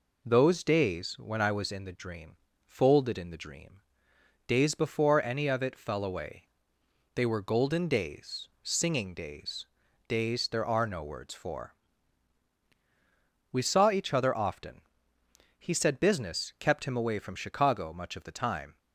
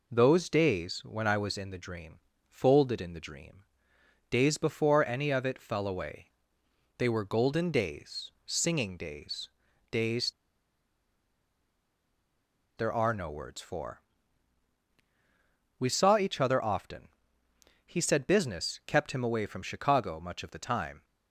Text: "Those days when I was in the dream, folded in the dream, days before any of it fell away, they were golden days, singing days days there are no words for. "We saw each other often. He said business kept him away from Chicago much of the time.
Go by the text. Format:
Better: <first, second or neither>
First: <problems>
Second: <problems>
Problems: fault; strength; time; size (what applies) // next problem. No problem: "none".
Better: first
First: pauses between "days" and "days"; at 9.6 s; 0.42 s long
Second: pauses between "days" and "days"; at 9.4 s; 0.42 s long // pauses between "days" and "there"; strong; at 10.3 s; 2.4 s long